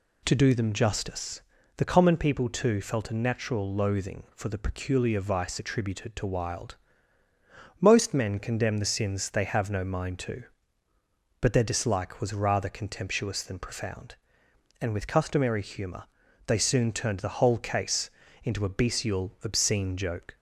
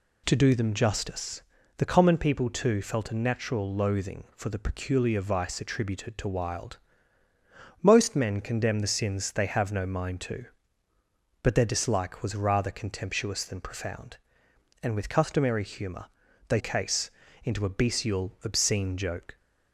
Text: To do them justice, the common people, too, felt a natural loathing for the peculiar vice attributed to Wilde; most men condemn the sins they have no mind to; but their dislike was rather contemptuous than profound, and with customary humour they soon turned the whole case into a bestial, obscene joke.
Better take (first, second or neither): first